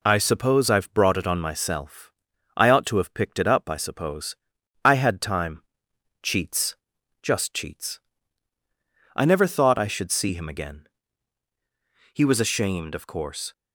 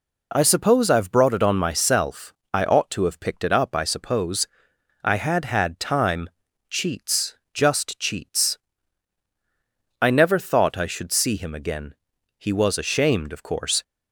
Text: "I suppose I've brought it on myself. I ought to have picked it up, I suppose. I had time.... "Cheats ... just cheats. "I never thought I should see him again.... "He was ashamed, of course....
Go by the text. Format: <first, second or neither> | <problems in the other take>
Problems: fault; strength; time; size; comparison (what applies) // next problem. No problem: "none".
first | says "had" twice; at 5.4 s